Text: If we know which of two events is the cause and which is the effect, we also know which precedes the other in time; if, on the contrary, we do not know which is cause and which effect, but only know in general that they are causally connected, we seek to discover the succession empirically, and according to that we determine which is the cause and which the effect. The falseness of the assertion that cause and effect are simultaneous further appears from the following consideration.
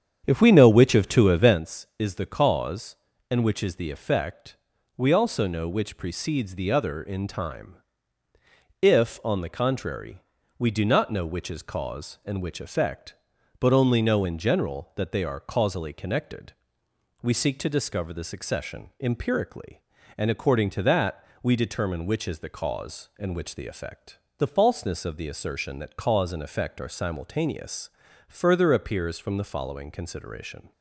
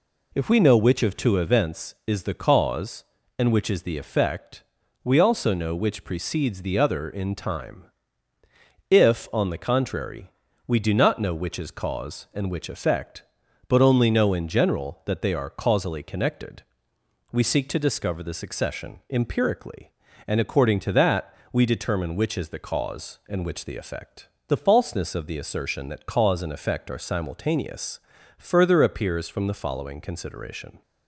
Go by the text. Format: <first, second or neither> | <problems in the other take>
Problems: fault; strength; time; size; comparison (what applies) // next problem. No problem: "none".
second | starts louder than the rest; strong; until 1.6 s; 8.5 dB // pauses between "that" and "we"; slight; at 21.2 s; 0.18 s long; slight in the second // pauses between "simultaneous" and "further"; at 27.8 s; 0.38 s long; also in the second